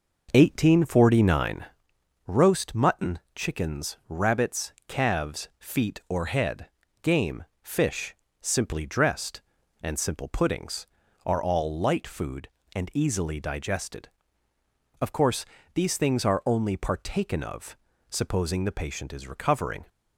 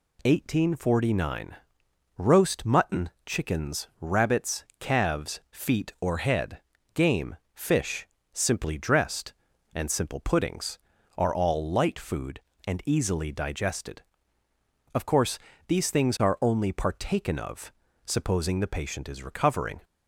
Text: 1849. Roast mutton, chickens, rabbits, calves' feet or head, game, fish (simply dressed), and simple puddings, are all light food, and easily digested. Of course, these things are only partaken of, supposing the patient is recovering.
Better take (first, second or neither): second